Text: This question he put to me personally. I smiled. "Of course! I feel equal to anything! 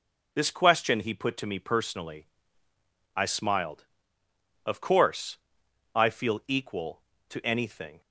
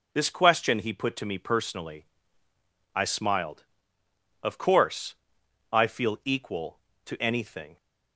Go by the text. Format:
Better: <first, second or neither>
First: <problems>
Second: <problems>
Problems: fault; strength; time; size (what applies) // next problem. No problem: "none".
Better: neither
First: none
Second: none